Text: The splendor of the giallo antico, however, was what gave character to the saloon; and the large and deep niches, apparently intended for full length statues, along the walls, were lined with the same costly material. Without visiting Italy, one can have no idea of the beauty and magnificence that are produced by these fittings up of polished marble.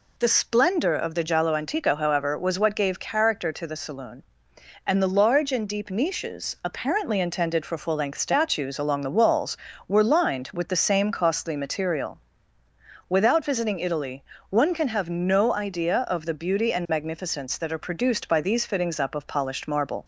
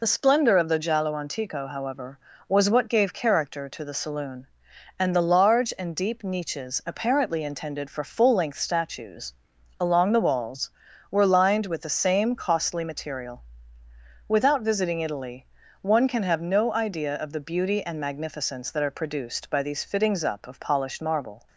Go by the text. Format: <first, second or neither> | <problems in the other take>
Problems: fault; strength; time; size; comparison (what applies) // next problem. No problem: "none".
first | loses the start of "The"; at 0.0 s; 35 ms